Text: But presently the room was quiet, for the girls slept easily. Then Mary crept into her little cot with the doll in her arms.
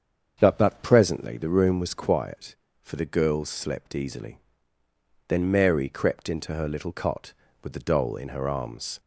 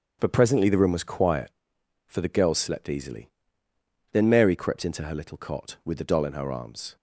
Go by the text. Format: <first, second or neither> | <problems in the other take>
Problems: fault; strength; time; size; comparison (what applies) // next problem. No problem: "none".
second | starts louder than the rest; strong; until 1.4 s; 7 dB; strong in the second // says "But" twice; at 0.5 s